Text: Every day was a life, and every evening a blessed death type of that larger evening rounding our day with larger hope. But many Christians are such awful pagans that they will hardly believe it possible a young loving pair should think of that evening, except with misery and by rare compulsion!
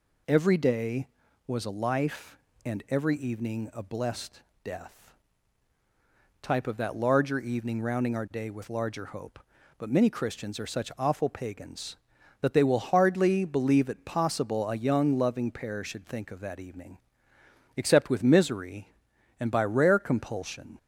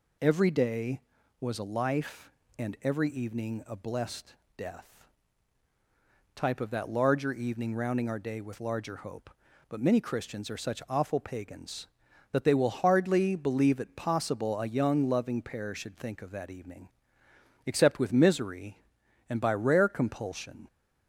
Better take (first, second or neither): neither